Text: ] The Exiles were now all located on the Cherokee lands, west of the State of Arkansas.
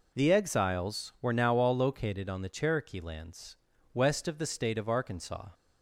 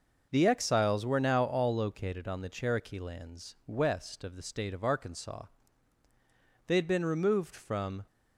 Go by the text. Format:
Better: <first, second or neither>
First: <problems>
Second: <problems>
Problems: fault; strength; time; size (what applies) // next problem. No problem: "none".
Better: first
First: none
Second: goes on to say "They had been removed from"; from 6.6 s on; 1.3 s long